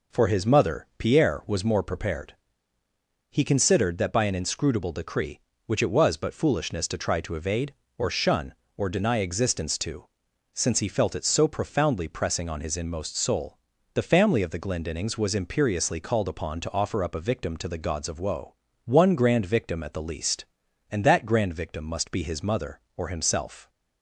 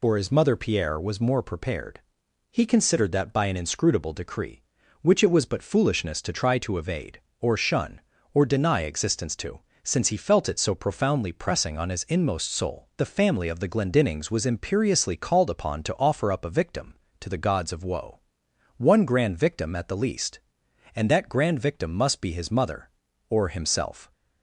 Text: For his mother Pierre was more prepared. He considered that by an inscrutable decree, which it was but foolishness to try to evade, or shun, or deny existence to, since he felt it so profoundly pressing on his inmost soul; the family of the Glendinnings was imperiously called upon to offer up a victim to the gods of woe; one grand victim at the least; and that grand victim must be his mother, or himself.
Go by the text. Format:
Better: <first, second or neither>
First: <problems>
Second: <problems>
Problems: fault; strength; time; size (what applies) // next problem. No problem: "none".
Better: first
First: none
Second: loses the start of "For"; at 0.0 s; 50 ms